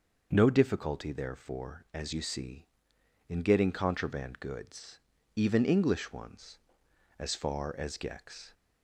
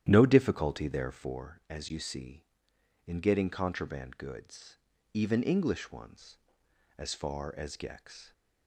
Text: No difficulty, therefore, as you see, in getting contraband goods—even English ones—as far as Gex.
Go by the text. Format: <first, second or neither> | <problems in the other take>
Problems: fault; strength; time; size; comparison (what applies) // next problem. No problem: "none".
first | starts louder than the rest; strong; until 1.5 s; 11 dB